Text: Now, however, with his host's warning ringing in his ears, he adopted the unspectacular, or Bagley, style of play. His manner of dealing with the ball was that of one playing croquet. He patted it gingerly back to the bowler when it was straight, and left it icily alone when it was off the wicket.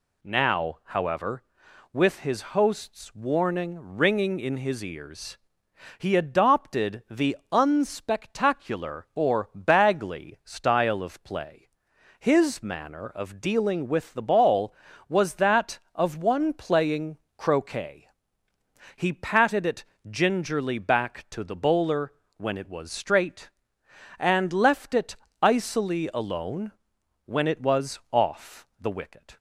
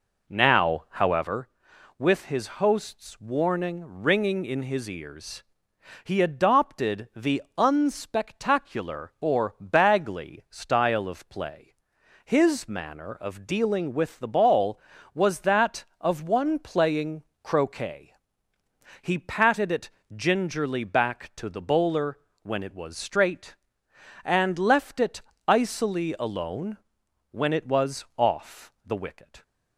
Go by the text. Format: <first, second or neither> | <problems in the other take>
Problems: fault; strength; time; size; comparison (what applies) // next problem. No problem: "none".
first | starts louder than the rest; slight; until 1.4 s; 3.5 dB // pauses between "the" and "unspectacular"; slight; at 7.4 s; 0.16 s long; slight in the first // pauses between "playing" and "croquet"; slight; at 17.2 s; 0.20 s long; slight in the first // pauses between "it" and "gingerly"; slight; at 19.9 s; 0.24 s long; slight in the first // pauses between "bowler" and "when"; slight; at 22.1 s; 0.24 s long; slight in the first // pauses between "it" and "icily"; slight; at 25.2 s; 0.26 s long; slight in the first // pauses between "alone" and "when"; noticeable; at 26.7 s; 0.52 s long; noticeable in the first